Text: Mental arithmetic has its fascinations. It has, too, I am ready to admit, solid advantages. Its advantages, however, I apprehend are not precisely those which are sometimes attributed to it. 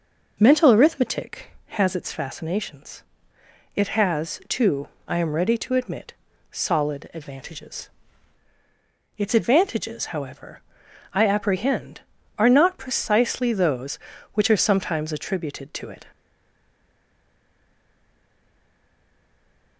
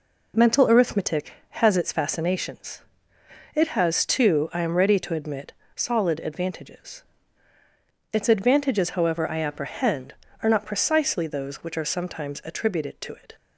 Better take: second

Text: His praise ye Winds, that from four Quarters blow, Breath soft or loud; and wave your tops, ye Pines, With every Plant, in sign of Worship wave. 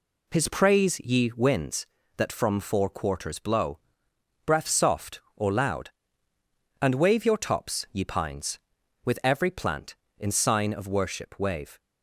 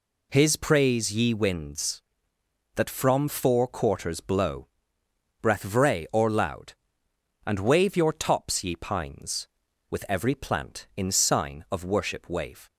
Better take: first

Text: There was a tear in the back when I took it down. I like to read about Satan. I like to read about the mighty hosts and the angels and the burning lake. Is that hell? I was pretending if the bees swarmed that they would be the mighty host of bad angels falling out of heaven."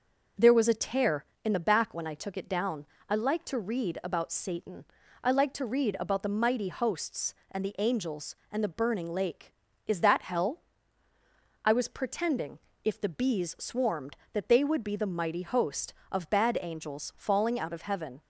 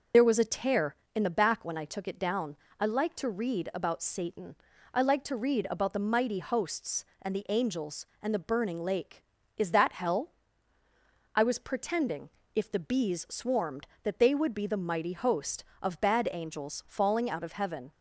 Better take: first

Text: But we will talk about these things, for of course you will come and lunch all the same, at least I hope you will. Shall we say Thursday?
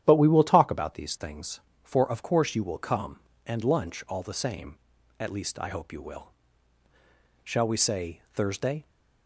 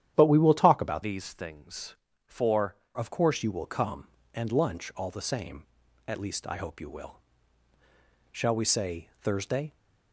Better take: first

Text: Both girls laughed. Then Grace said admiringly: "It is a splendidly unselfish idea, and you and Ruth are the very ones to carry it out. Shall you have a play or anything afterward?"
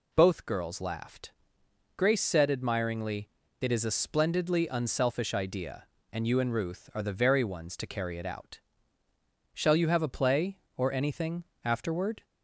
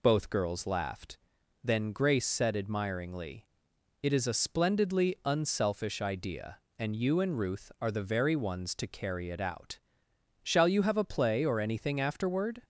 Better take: second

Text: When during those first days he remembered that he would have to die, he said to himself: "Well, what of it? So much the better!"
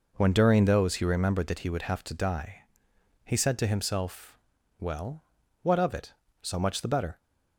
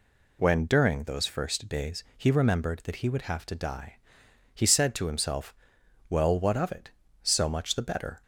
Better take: second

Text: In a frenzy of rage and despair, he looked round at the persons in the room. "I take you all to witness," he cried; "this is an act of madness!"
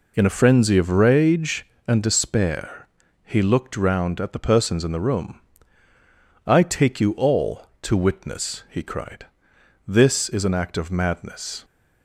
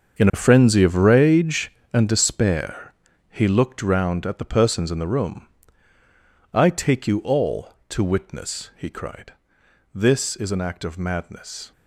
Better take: first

